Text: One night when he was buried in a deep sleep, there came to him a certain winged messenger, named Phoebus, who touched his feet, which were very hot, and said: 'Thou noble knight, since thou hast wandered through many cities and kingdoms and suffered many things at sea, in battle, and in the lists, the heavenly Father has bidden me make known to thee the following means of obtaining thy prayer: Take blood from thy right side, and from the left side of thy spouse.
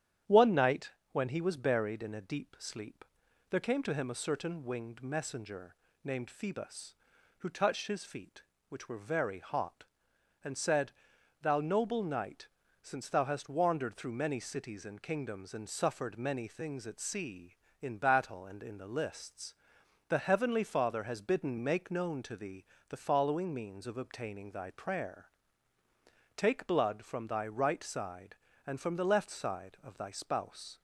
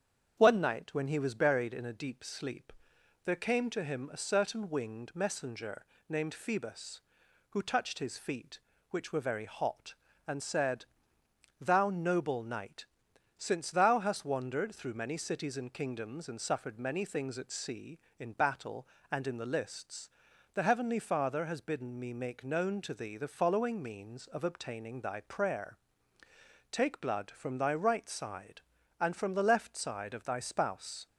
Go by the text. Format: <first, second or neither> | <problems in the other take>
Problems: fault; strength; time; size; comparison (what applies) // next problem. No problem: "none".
second | starts louder than the rest; strong; until 1.5 s; 10 dB; strong in the second // pauses between "night" and "when"; slight; at 0.8 s; 0.22 s long // skips "me"; at 21.5 s // pauses between "thee" and "the"; slight; at 22.6 s; 0.24 s long